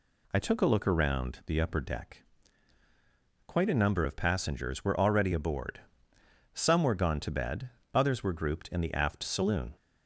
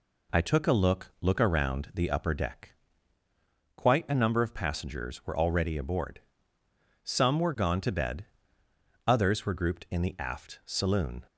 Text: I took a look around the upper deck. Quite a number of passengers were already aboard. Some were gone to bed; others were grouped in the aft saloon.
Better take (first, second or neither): first